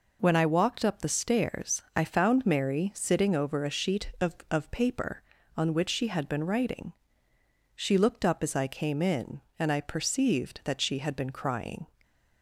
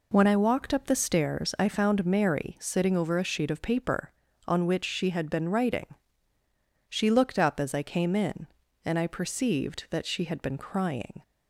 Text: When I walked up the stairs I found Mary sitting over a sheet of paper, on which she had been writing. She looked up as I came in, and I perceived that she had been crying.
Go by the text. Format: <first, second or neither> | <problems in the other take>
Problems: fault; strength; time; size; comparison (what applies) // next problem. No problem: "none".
second | pauses between "stairs" and "I"; slight; at 1.8 s; 0.16 s long // says "of" twice; at 4.5 s